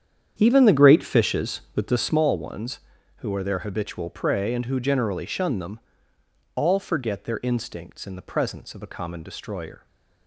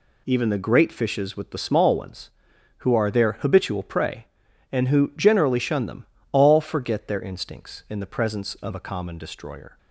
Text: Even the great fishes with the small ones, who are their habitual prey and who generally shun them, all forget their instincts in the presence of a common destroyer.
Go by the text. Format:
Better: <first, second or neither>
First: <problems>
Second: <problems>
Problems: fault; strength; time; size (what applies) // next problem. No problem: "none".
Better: second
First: starts louder than the rest; strong; until 2.2 s; 8.5 dB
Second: none